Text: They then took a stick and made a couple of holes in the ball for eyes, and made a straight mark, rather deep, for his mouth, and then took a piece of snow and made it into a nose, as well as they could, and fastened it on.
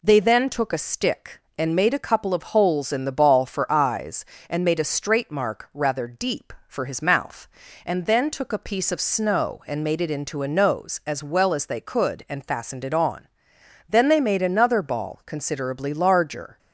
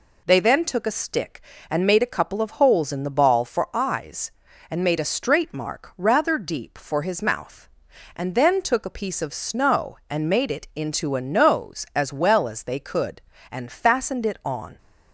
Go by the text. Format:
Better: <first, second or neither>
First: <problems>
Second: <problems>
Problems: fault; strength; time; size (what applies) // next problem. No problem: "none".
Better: second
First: goes on to say "Then they made another ball considerably larger"; strong; from 13.8 s on; 2.7 s long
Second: none